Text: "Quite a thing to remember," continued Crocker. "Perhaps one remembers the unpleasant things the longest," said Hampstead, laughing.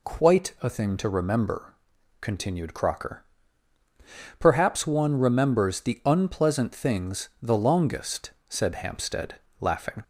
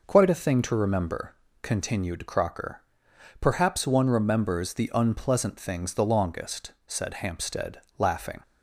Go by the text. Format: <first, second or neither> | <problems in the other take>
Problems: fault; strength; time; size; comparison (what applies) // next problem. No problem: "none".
neither | none